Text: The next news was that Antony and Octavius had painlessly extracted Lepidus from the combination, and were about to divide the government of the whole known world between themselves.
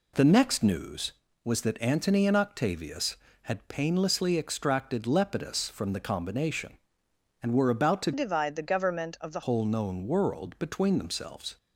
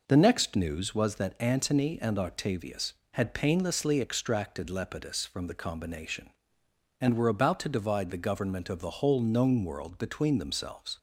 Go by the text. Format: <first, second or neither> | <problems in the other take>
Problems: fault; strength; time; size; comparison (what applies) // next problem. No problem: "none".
second | changes voice from "divide" to "the"; from 8.1 to 9.4 s; 1.3 s long